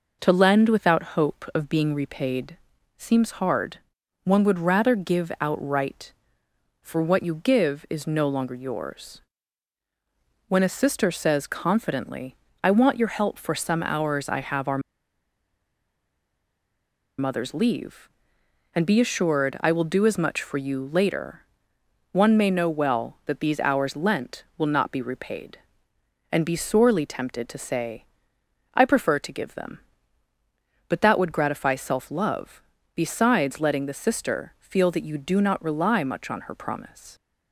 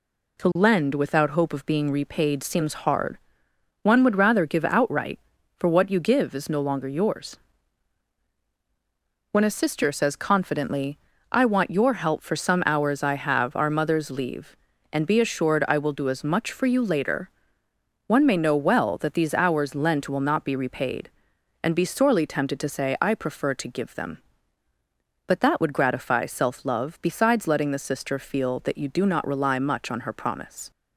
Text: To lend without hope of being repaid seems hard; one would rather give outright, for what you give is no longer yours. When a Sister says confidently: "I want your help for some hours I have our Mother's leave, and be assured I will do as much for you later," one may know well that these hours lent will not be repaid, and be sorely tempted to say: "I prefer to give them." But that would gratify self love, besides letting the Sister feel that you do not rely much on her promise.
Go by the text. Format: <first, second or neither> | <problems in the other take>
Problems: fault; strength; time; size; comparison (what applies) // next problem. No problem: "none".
second | pauses between "repaid" and "seems"; at 2.5 s; 0.40 s long // pauses between "our" and "Mother's"; strong; at 14.8 s; 2.3 s long